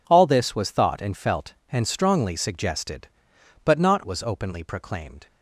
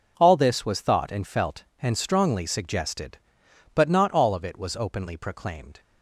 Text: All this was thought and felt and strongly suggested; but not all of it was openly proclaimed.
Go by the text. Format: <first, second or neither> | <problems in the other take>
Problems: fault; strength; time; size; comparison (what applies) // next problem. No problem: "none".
second | skips "all of it"; at 4.0 s